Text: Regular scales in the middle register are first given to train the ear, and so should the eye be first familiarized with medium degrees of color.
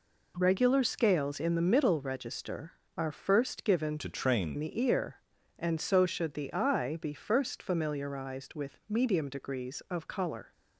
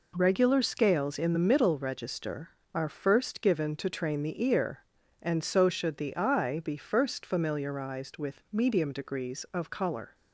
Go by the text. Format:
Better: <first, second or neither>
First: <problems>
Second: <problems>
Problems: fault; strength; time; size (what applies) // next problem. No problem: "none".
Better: second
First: changes voice from "to" to "train"; from 3.9 to 4.5 s; 0.6 s long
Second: none